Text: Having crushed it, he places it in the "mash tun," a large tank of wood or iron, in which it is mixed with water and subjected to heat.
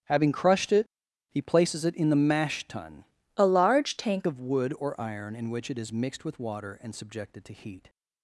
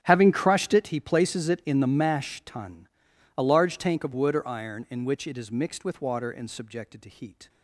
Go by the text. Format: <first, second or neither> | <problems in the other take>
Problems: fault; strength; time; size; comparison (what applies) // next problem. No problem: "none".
second | starts louder than the rest; strong; until 1.4 s; 10 dB; strong in the second // changes voice from "a" to "tank"; from 3.3 to 4.2 s; 0.9 s long